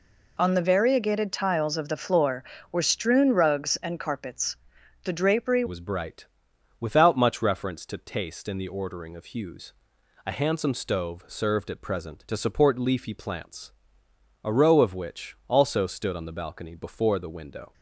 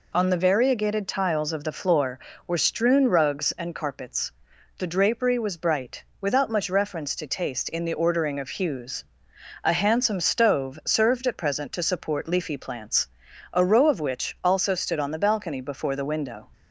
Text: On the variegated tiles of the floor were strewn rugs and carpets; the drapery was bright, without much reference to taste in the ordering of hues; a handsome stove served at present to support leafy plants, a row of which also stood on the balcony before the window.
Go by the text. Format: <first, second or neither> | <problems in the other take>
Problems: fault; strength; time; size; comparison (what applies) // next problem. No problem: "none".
second | changes voice at "was"; from 5.6 s on; 12.1 s long